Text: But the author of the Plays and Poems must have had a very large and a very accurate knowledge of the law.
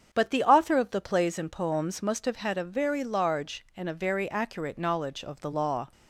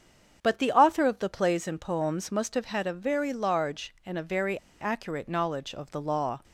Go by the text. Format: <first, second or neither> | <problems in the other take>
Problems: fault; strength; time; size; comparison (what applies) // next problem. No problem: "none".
first | starts louder than the rest; strong; until 1.4 s; 7 dB; strong in the first // pauses between "very" and "accurate"; slight; at 4.5 s; 0.22 s long